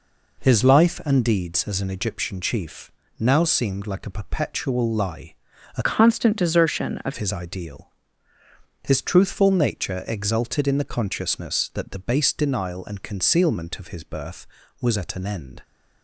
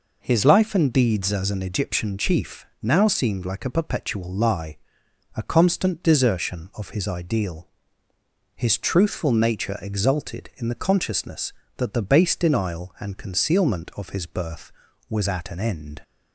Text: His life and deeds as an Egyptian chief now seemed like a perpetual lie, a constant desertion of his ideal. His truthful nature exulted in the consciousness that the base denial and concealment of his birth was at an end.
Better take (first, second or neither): second